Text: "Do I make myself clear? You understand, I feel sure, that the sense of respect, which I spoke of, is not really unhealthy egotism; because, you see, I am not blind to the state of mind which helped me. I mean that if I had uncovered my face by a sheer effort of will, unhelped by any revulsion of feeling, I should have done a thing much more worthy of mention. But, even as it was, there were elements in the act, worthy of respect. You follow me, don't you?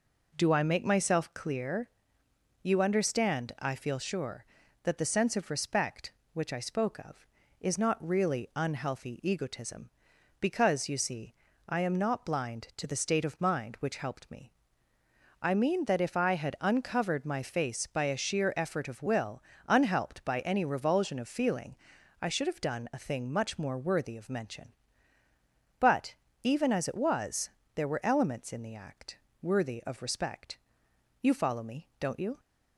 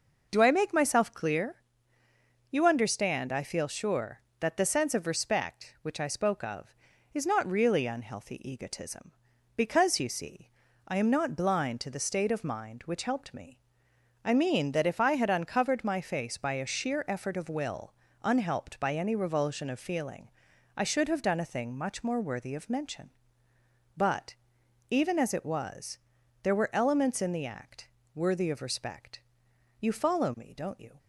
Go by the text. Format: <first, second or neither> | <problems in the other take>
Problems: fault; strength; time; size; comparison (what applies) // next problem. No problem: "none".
neither | none